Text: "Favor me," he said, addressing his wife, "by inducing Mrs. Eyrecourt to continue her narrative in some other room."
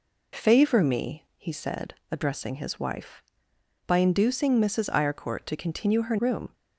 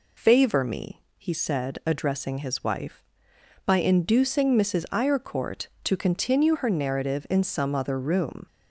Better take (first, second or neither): second